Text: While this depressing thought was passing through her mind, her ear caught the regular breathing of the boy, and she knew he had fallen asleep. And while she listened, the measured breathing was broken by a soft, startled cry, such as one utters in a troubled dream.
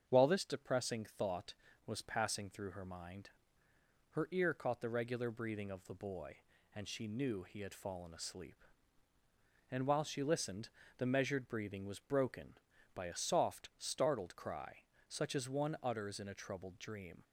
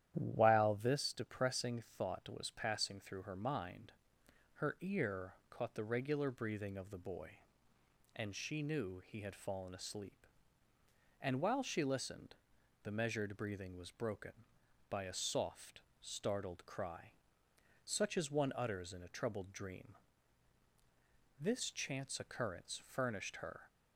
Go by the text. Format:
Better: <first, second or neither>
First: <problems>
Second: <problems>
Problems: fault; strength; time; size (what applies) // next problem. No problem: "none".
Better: first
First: starts louder than the rest; strong; until 1.1 s; 7.5 dB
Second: starts louder than the rest; strong; until 1.1 s; 11 dB // pauses between "ear" and "caught"; slight; at 5.3 s; 0.16 s long // goes on to say "This chance occurrence furnished her"; strong; from 21.4 s on; 2.2 s long